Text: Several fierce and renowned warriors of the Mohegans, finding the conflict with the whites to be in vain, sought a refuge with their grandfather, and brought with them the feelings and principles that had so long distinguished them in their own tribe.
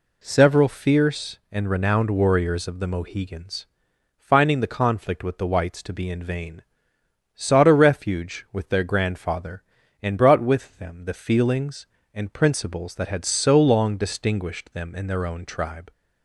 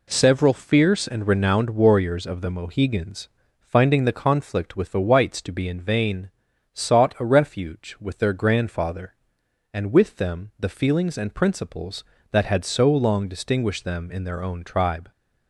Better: first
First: none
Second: skips "brought"; at 9.9 s

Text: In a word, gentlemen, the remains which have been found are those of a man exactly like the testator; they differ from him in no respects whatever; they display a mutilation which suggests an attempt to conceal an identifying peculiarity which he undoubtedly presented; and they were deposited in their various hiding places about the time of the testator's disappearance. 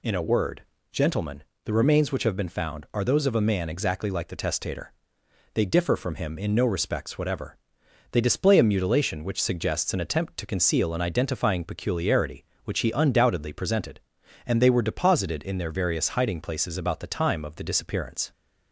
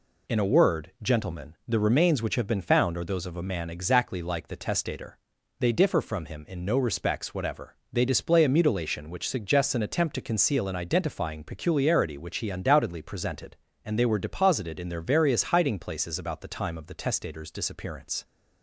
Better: second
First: skips "testator's"; at 17.6 s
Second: none

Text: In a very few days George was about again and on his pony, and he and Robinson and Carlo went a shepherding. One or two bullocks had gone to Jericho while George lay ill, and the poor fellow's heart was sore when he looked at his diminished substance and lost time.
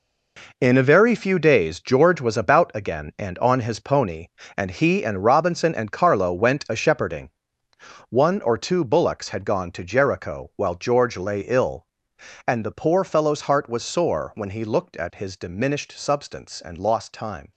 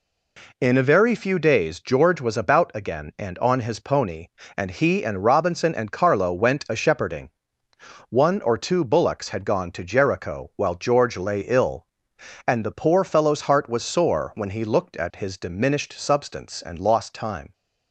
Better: second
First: gets quieter; strong; throughout; 10.5 dB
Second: none

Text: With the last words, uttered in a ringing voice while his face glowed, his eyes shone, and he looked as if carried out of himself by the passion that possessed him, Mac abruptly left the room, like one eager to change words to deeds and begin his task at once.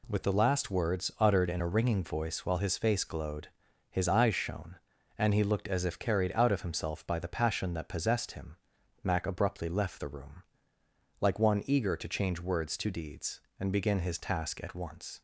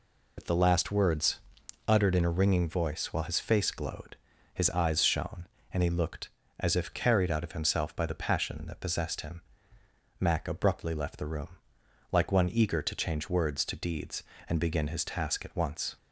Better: first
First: none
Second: loses the start of "With"; at 0.3 s; 35 ms

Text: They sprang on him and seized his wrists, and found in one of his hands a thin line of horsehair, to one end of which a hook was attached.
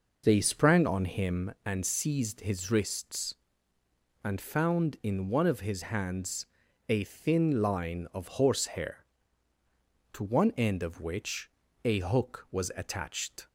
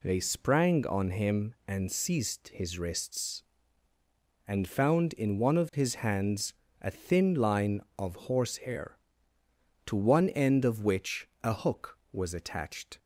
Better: second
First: starts louder than the rest; noticeable; until 1.6 s; 5 dB // pauses between "hands" and "a"; at 6.4 s; 0.42 s long // pauses between "which" and "a"; slight; at 11.4 s; 0.34 s long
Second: pauses between "hands" and "a"; slight; at 6.5 s; 0.26 s long // pauses between "which" and "a"; slight; at 11.2 s; 0.16 s long

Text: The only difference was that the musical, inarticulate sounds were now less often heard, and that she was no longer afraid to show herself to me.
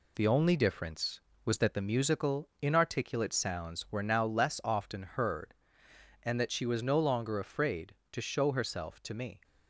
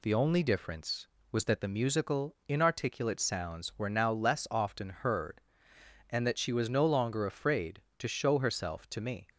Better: second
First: gets quieter; noticeable; throughout; 4 dB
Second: none

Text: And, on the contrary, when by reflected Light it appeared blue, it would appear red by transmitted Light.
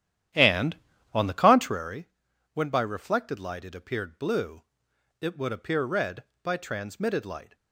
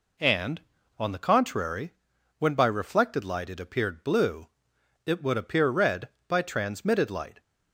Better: second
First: starts louder than the rest; strong; until 1.8 s; 11 dB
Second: none

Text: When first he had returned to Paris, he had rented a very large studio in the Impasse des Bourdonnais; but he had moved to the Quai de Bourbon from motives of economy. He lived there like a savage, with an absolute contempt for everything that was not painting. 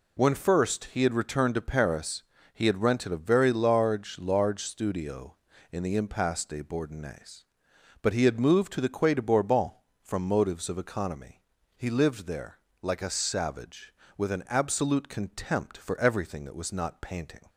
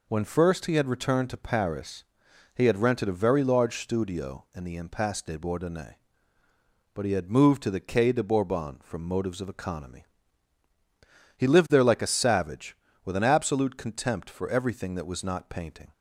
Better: second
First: says "large" twice; at 4.1 s // pauses between "there" and "like"; slight; at 12.5 s; 0.24 s long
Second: none

